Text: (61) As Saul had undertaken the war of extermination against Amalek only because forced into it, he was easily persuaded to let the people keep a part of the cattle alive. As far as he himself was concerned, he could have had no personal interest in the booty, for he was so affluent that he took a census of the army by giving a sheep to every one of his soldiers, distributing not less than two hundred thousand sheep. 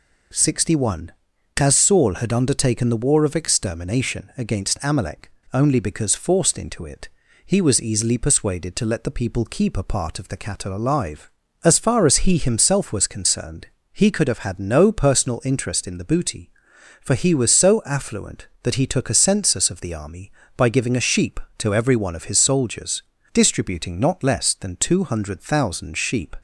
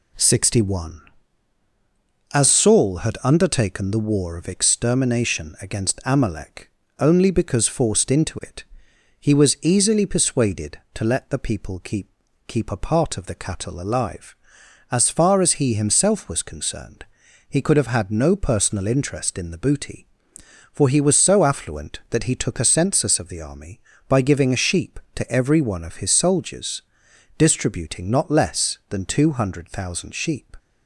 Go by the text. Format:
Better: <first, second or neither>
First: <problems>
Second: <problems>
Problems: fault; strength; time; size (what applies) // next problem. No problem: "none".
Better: first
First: pauses between "Amalek" and "only"; slight; at 5.3 s; 0.22 s long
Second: pauses between "Amalek" and "only"; slight; at 6.7 s; 0.30 s long // says "keep" twice; at 12.4 s